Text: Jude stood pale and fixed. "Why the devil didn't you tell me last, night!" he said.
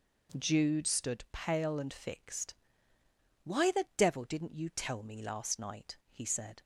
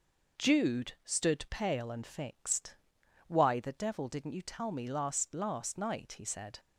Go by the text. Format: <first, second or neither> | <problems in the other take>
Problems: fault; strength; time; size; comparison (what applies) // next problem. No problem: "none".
first | says "last" twice; at 5.3 s